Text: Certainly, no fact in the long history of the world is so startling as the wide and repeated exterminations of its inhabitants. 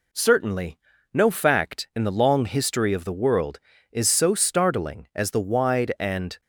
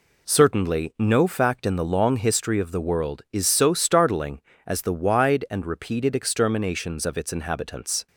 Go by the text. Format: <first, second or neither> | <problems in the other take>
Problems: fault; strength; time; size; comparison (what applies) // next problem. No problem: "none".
second | stops before "repeated exterminations of its inhabitants"; at 6.4 s